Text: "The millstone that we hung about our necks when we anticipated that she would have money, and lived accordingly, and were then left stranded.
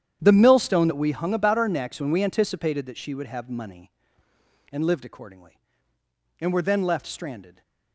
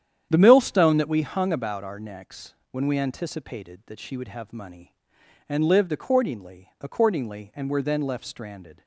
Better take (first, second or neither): first